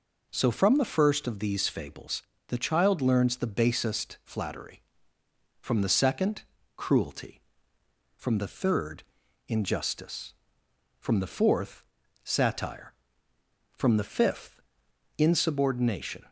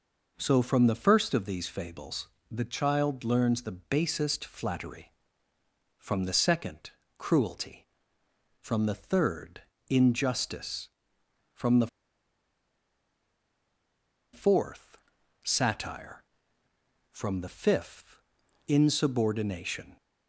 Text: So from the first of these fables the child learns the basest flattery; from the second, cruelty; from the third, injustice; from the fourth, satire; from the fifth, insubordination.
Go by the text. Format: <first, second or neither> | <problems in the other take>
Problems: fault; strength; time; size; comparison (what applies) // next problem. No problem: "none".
first | pauses between "fables" and "the"; slight; at 2.2 s; 0.24 s long; slight in the first // pauses between "the" and "fourth"; strong; at 11.8 s; 2.4 s long